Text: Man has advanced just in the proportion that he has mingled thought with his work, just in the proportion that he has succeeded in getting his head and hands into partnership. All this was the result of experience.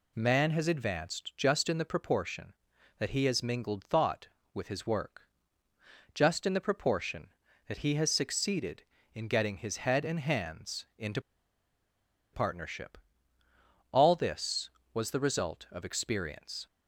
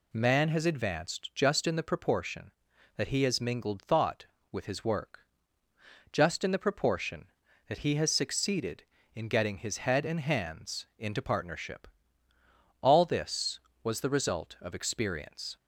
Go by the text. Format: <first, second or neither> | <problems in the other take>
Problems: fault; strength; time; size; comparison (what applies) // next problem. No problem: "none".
second | pauses between "into" and "partnership"; at 11.1 s; 1.1 s long